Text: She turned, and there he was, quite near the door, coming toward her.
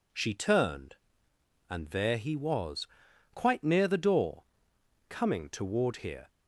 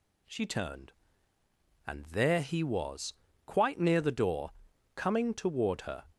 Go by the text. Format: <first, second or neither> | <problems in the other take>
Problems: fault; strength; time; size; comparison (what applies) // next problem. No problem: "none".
second | says "here" for "her"; at 5.9 s